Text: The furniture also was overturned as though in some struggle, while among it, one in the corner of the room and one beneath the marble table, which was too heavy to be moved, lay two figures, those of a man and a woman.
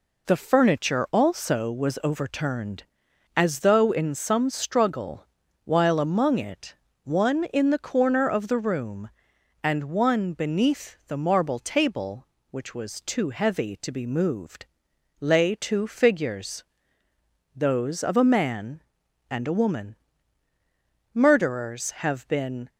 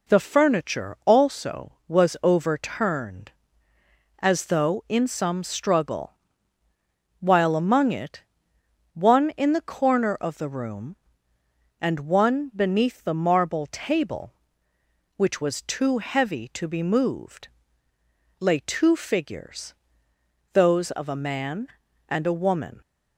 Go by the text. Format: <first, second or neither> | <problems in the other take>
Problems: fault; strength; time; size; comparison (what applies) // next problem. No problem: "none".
second | goes on to say "Murderers have been"; from 21.1 s on; 1.5 s long